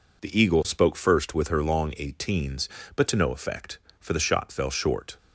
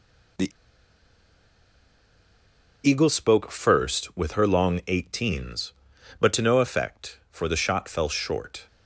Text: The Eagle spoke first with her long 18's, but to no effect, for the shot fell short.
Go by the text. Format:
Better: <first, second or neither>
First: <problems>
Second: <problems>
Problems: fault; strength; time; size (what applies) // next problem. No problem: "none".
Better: first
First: none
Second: pauses between "The" and "Eagle"; strong; at 0.5 s; 2.3 s long